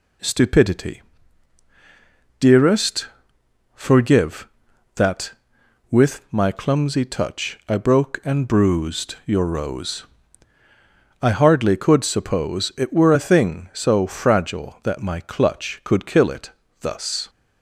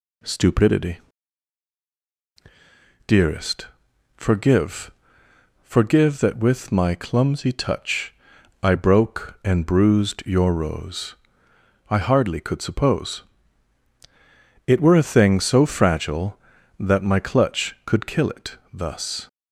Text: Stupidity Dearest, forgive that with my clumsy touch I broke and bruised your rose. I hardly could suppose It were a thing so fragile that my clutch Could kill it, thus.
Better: first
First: pauses between "Stupidity" and "Dearest"; strong; at 1.0 s; 1.3 s long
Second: pauses between "Stupidity" and "Dearest"; strong; at 0.9 s; 2.0 s long // says "forgive" twice; at 5.6 s // pauses between "touch" and "I"; noticeable; at 8.1 s; 0.48 s long // pauses between "suppose" and "It"; strong; at 13.2 s; 1.4 s long

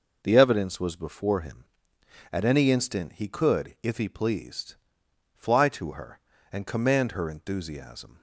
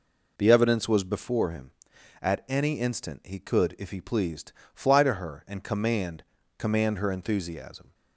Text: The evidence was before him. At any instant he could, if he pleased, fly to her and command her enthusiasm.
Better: first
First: none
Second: says "command" twice; at 6.5 s

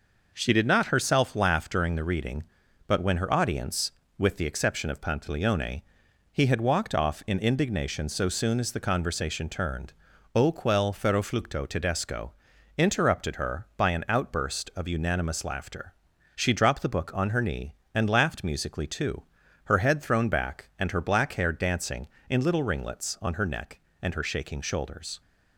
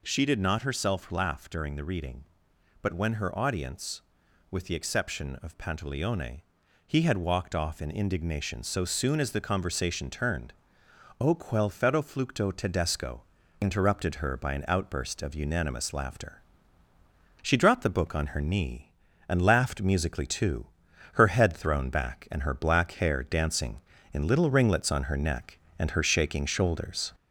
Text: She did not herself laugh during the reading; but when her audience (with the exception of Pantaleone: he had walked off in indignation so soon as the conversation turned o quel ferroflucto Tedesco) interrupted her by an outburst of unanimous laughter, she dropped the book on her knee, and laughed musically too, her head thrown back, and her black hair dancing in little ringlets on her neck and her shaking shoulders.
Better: first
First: pauses between "turned" and "o"; at 9.9 s; 0.42 s long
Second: gets louder; slight; throughout; 2.5 dB // pauses between "turned" and "o"; noticeable; at 10.5 s; 0.66 s long

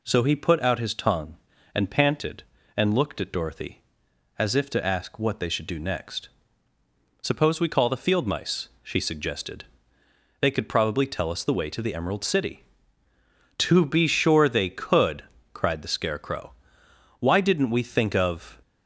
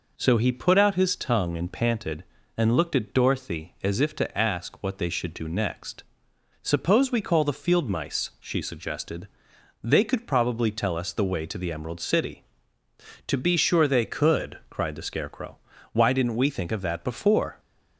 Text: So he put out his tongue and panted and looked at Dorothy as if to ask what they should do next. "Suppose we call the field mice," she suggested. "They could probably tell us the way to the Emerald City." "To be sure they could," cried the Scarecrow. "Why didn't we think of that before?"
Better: second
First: stops before "that before"; at 18.6 s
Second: none

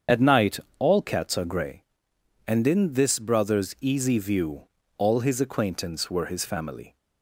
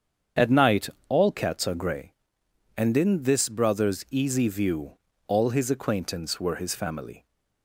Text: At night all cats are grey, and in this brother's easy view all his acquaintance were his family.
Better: second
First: loses the start of "At"; at 0.0 s; 25 ms // starts louder than the rest; strong; until 1.2 s; 7.5 dB // pauses between "night" and "all"; slight; at 0.5 s; 0.20 s long // pauses between "view" and "all"; slight; at 4.6 s; 0.34 s long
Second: starts louder than the rest; strong; until 1.5 s; 7.5 dB // pauses between "night" and "all"; slight; at 0.8 s; 0.20 s long // pauses between "view" and "all"; slight; at 4.9 s; 0.34 s long

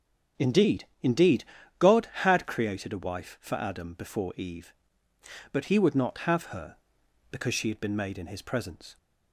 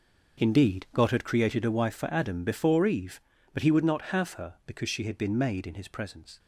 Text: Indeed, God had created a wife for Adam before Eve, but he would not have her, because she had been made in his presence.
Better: second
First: starts louder than the rest; until 1.8 s; 7 dB // says "Indeed" twice; at 1.0 s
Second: none

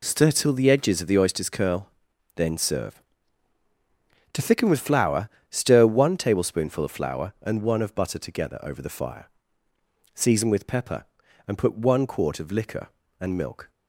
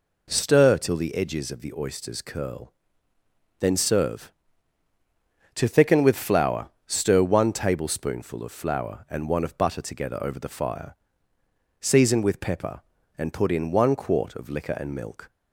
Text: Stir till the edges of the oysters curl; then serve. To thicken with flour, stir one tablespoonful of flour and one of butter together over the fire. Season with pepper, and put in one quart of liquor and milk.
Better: second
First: skips "in"; at 11.7 s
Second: none

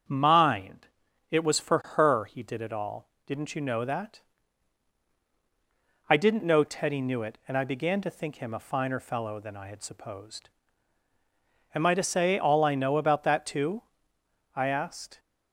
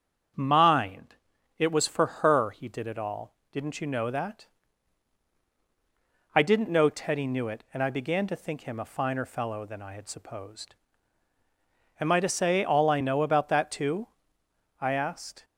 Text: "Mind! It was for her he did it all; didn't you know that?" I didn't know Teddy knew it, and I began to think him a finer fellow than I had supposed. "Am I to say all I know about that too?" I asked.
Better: neither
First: starts louder than the rest; strong; until 1.5 s; 7 dB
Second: starts louder than the rest; until 1.7 s; 7 dB

